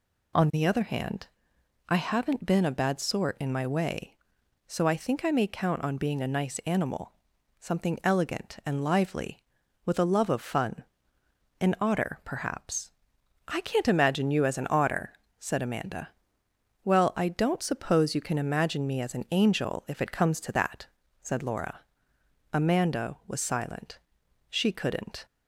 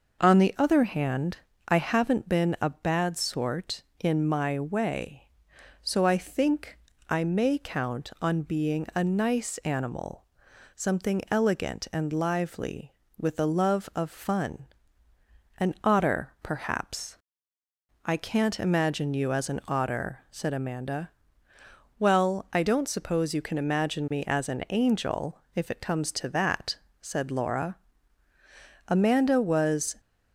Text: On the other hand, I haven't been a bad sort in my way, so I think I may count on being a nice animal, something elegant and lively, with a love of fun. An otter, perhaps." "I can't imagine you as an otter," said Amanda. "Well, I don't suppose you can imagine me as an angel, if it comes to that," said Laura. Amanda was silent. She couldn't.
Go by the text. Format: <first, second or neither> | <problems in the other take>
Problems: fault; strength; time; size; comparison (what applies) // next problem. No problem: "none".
first | pauses between "think" and "I"; slight; at 6.7 s; 0.32 s long // stops before "silent She couldn't"; at 29.9 s